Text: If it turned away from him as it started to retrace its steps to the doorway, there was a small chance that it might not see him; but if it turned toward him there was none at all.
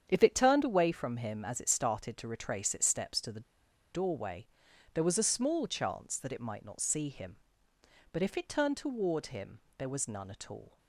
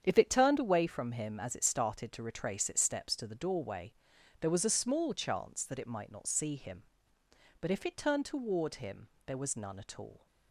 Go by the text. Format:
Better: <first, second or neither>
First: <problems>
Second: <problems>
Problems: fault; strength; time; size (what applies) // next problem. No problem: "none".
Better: second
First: starts louder than the rest; strong; until 1.1 s; 8 dB // pauses between "the" and "doorway"; noticeable; at 3.4 s; 0.51 s long // pauses between "him" and "there"; slight; at 9.5 s; 0.16 s long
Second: starts louder than the rest; strong; until 1.0 s; 8 dB // pauses between "him" and "there"; slight; at 9.0 s; 0.16 s long